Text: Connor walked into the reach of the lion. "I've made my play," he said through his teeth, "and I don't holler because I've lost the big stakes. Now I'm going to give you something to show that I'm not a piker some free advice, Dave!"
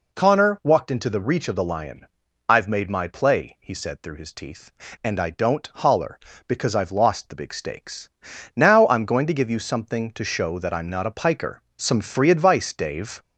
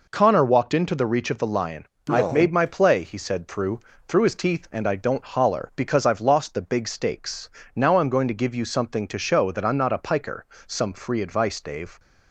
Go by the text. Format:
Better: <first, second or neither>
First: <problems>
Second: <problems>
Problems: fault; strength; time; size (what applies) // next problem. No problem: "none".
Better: first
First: pauses between "piker" and "some"; slight; at 11.6 s; 0.16 s long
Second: says "through" twice; at 4.0 s // pauses between "piker" and "some"; slight; at 10.4 s; 0.20 s long